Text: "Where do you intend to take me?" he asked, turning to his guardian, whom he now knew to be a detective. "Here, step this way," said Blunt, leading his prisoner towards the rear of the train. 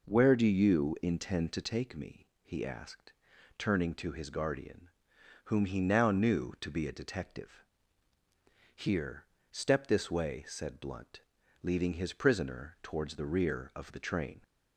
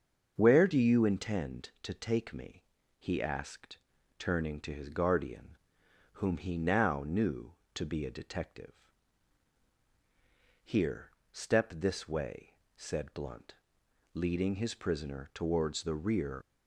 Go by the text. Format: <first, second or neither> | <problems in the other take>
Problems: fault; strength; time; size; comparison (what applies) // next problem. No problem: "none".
first | starts louder than the rest; until 1.3 s; 6.5 dB // stops before "of the train"; at 16.4 s